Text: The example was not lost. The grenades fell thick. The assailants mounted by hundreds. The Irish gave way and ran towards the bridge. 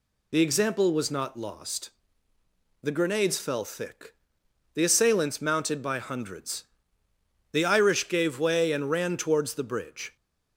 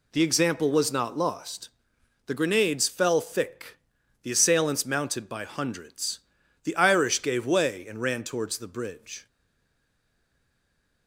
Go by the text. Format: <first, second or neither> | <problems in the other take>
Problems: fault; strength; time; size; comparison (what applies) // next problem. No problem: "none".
first | stays silent after the last word; noticeable; from 9.2 s on; 1.8 s long